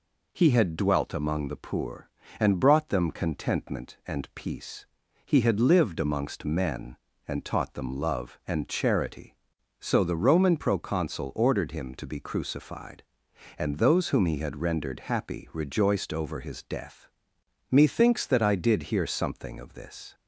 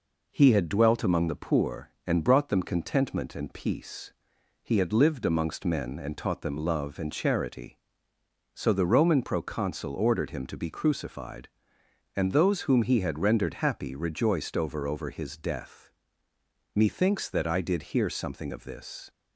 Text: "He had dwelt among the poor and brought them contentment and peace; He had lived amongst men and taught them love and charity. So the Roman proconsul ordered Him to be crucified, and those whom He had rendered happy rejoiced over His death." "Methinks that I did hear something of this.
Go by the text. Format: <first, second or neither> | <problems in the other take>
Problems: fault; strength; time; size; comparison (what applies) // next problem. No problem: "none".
first | says "over" twice; at 14.8 s